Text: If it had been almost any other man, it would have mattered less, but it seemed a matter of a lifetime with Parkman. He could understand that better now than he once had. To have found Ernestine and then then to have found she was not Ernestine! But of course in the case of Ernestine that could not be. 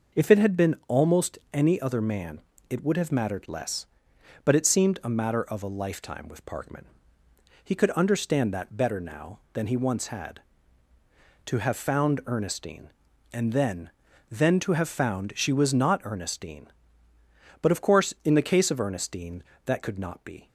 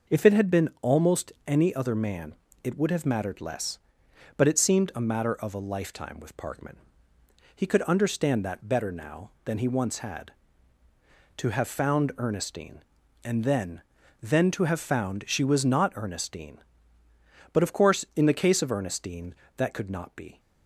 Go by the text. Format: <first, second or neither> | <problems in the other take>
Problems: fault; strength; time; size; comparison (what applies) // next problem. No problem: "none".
neither | pauses between "almost" and "any"; slight; the same in both // pauses between "then" and "then"; the same in both